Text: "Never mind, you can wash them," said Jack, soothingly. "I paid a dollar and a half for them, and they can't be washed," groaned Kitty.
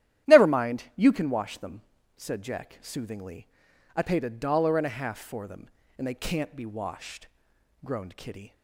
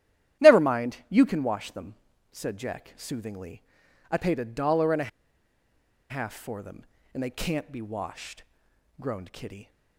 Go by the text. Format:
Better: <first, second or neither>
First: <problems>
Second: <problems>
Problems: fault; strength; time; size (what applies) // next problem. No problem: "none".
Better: first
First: starts louder than the rest; strong; until 1.3 s; 12 dB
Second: starts louder than the rest; strong; until 1.5 s; 12 dB // pauses between "a" and "half"; at 5.0 s; 0.99 s long